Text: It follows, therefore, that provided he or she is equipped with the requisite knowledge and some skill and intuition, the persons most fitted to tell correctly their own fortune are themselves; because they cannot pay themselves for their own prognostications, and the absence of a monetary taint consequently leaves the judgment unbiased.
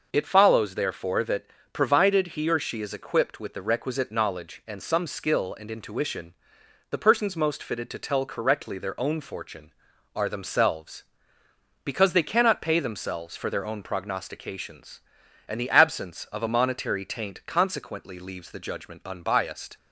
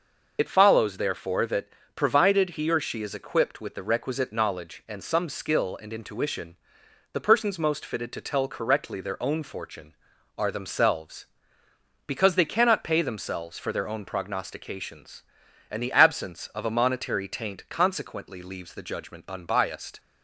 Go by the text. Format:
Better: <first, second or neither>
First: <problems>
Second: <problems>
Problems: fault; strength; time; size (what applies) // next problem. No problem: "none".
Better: first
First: pauses between "that" and "provided"; slight; at 1.4 s; 0.26 s long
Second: loses the start of "It"; at 0.3 s; 45 ms // pauses between "that" and "provided"; slight; at 1.6 s; 0.26 s long